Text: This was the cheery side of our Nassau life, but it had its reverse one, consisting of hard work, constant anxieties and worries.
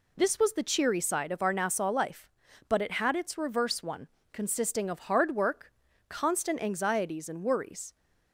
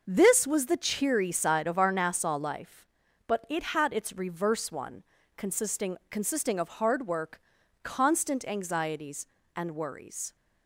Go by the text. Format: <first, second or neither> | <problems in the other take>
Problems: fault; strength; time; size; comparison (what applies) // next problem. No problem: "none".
first | says "consisting" twice; at 6.1 s